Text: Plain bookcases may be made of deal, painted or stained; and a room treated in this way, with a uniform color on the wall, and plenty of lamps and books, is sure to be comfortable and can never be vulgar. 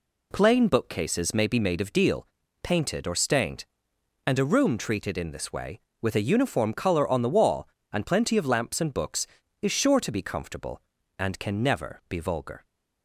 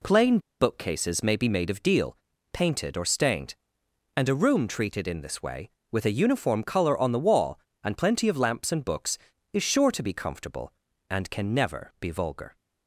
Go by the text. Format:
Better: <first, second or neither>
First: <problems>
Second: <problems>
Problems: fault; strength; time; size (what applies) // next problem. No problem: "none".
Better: first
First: none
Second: pauses between "Plain" and "bookcases"; slight; at 0.3 s; 0.21 s long